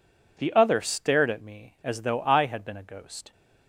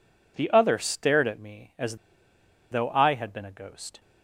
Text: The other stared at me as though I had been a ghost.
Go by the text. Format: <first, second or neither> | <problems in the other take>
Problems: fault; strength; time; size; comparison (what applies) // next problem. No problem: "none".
first | pauses between "as" and "though"; noticeable; at 1.9 s; 0.74 s long